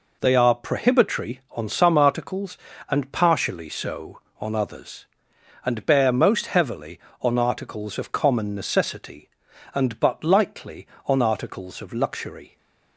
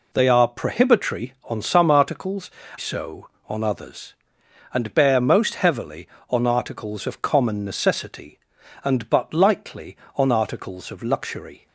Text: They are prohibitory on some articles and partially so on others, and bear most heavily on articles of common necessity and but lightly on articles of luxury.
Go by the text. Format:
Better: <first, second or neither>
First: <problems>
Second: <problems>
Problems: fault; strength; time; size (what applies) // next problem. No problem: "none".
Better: first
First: none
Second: skips "and partially"; at 2.6 s